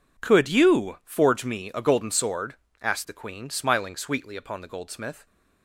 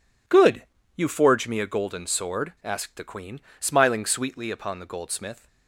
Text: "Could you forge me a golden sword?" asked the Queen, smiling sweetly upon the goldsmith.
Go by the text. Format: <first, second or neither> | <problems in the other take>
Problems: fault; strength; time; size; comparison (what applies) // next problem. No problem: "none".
first | says "Good" for "Could"; at 0.2 s